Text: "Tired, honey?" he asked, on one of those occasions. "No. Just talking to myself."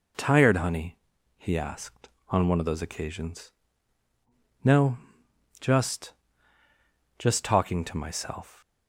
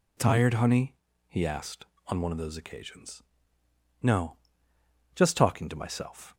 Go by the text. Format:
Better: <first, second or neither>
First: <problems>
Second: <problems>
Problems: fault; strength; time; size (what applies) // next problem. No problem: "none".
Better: second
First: says "Just" twice; at 7.1 s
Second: none